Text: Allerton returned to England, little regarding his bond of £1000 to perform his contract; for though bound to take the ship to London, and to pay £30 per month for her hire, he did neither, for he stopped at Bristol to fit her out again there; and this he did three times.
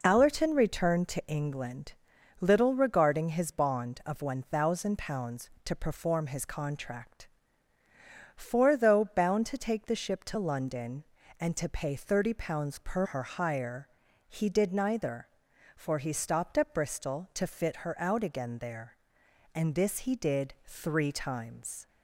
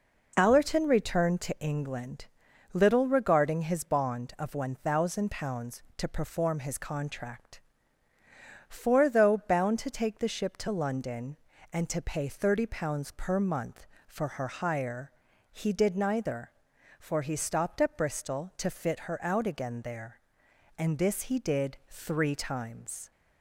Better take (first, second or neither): second